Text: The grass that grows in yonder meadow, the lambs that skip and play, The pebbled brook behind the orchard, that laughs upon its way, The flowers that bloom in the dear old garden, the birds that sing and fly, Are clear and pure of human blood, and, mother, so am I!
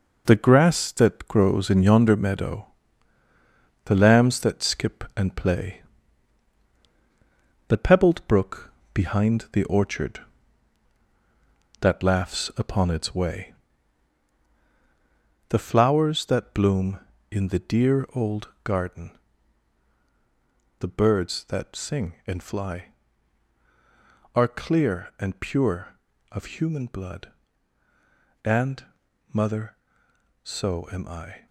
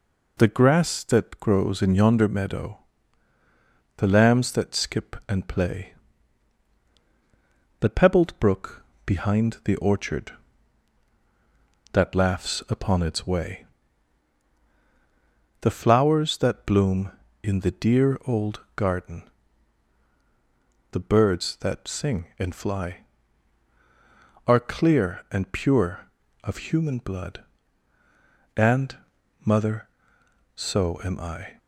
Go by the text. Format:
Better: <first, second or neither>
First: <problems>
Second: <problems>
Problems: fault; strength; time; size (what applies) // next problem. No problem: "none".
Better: second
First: gets quieter; strong; throughout; 7.5 dB // pauses between "brook" and "behind"; slight; at 8.7 s; 0.20 s long // pauses between "old" and "garden"; slight; at 18.4 s; 0.16 s long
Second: pauses between "brook" and "behind"; slight; at 8.8 s; 0.20 s long // pauses between "old" and "garden"; slight; at 18.6 s; 0.16 s long